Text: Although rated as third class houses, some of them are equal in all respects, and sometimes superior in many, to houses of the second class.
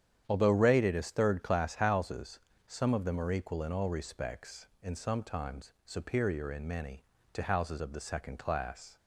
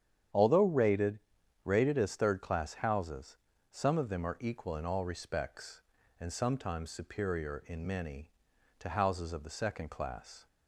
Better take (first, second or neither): first